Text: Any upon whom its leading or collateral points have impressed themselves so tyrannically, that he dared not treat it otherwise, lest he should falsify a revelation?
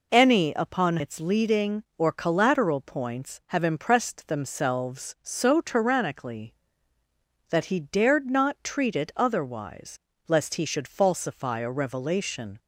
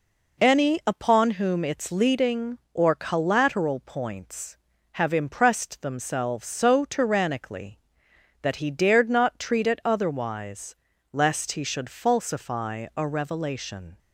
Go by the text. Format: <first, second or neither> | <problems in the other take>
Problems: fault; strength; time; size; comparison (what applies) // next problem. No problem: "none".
second | skips "whom"; at 0.9 s